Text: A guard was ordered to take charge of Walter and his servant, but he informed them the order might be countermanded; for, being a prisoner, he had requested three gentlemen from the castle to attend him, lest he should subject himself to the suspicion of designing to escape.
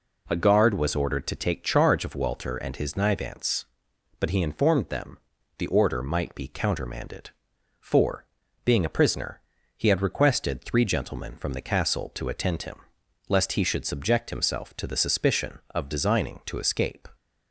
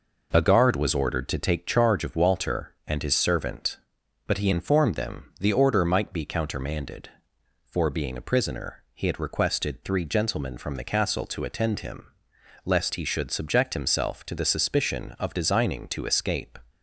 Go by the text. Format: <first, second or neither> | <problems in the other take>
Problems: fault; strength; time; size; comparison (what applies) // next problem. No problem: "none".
second | says "nivance" for "servant"; at 2.9 s // pauses between "them" and "the"; at 5.1 s; 0.40 s long